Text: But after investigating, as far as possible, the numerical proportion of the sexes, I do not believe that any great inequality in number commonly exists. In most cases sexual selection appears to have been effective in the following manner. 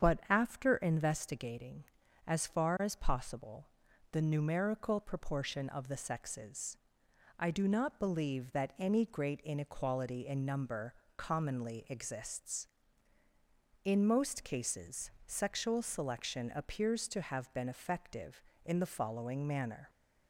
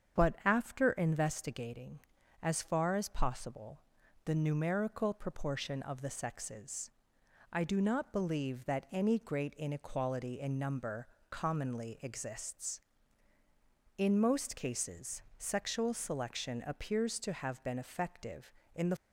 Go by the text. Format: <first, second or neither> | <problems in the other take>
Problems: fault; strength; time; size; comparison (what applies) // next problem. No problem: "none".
first | starts louder than the rest; strong; until 1.2 s; 8 dB; strong in the first // pauses between "number" and "commonly"; slight; at 11.0 s; 0.22 s long; slight in the first // pauses between "cases" and "sexual"; slight; at 15.2 s; 0.16 s long; slight in the first // stops before "following manner"; at 18.9 s